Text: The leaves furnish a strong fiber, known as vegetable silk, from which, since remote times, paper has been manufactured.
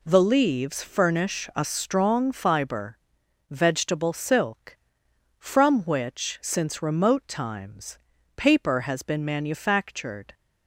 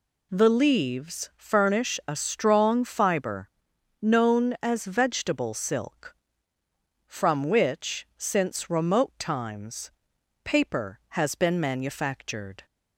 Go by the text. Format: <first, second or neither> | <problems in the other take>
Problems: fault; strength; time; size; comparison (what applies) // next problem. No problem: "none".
second | skips "known as"; at 3.2 s